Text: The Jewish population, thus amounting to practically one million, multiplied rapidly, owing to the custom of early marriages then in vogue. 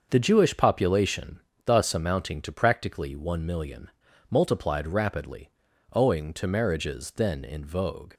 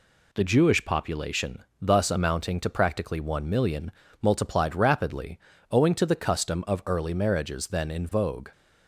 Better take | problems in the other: second | starts louder than the rest; until 1.1 s; 6.5 dB // skips "the custom of early"; at 6.4 s

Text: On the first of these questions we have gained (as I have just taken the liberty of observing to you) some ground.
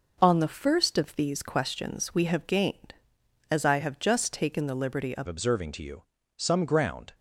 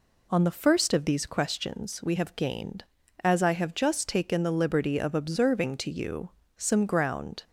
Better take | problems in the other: second | changes voice at "observing"; from 5.2 s on; 1.9 s long

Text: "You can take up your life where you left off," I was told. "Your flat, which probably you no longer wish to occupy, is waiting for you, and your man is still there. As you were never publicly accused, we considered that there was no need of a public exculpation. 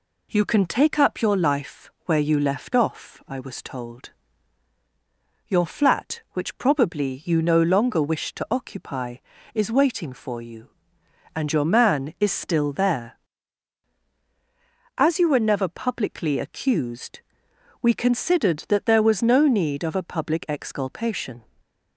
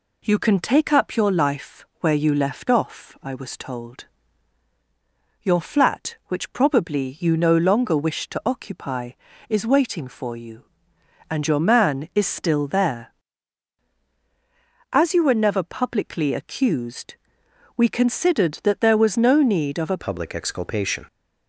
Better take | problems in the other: first | changes voice at "public"; from 20.0 s on; 1.0 s long

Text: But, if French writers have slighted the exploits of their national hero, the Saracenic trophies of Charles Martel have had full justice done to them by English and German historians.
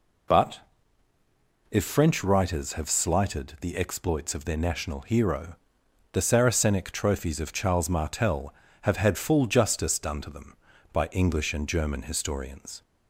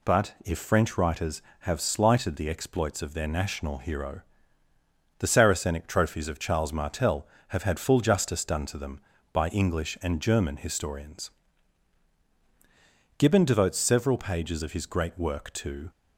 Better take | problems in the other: first | goes on to say "Gibbon devotes several pages of his great work to"; strong; from 13.1 s on; 2.7 s long

